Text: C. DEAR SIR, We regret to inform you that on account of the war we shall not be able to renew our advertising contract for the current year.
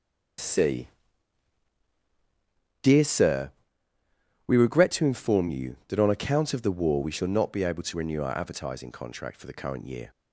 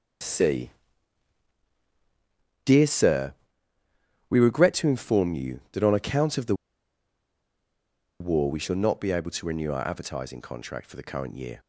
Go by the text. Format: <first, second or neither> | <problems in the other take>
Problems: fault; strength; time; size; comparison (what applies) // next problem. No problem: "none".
first | starts louder than the rest; strong; until 3.1 s; 7 dB; strong in the first // pauses between "the" and "war"; strong; at 6.5 s; 1.6 s long